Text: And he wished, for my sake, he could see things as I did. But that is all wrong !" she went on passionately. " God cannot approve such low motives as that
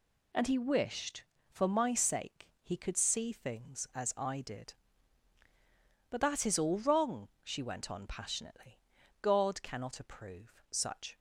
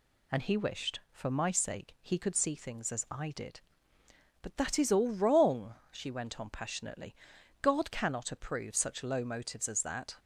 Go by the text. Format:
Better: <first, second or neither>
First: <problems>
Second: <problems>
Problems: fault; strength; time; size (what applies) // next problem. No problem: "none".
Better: second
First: stops before "low motives as that"; at 11.1 s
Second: none